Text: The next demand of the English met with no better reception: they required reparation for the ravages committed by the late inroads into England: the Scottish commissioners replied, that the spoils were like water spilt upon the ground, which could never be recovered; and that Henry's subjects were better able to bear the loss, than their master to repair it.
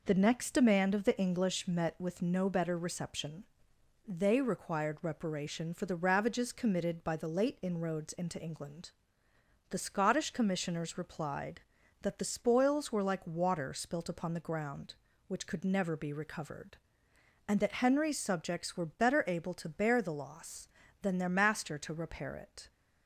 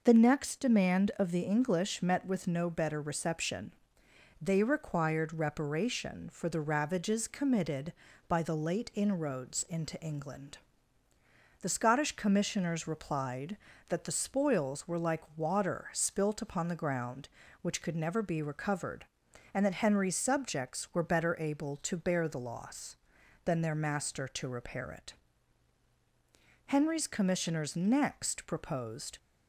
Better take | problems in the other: first | goes on to say "Henry's commissioners next proposed"; strong; from 26.6 s on; 2.5 s long

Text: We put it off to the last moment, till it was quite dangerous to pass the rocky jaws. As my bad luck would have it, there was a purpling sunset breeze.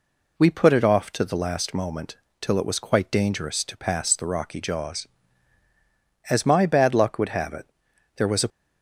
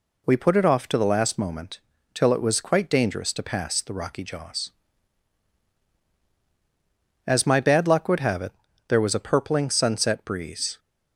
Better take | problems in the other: second | stops before "purpling sunset breeze"; at 8.4 s

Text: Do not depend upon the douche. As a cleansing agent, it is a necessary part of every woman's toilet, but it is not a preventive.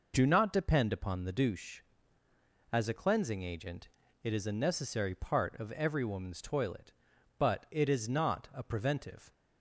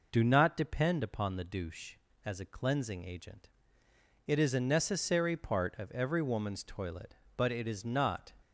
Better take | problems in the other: first | stops before "a preventive"; at 8.4 s

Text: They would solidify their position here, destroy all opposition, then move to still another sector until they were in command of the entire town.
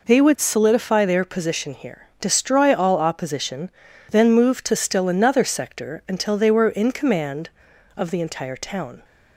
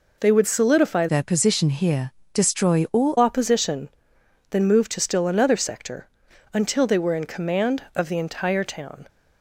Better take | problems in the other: first | changes voice from "their" to "all"; from 1.0 to 3.1 s; 2.1 s long // pauses between "sector" and "until"; noticeable; at 6.0 s; 0.46 s long

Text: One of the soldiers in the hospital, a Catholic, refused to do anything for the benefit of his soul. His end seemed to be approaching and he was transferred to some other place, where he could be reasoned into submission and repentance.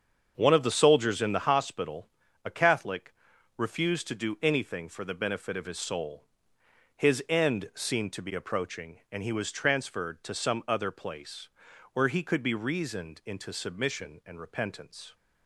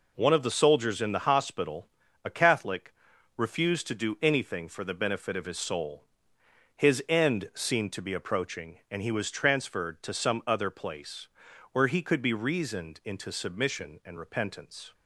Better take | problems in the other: second | starts louder than the rest; strong; until 1.6 s; 7 dB

